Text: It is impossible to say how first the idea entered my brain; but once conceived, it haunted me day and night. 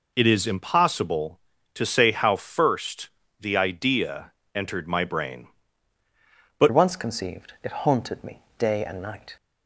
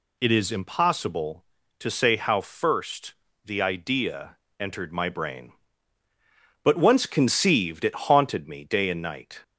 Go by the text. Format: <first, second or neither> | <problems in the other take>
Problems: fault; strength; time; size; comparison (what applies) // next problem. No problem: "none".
second | pauses between "first" and "the"; slight; at 3.0 s; 0.30 s long; slight in the second // pauses between "idea" and "entered"; slight; at 4.3 s; 0.20 s long; slight in the second // changes voice at "once"; from 6.7 s on; 2.6 s long // pauses between "me" and "day"; slight; at 8.4 s; 0.18 s long